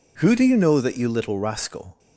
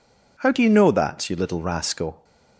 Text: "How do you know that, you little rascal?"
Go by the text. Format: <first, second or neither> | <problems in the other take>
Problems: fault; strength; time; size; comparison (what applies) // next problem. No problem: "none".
second | says "Who" for "How"; at 0.2 s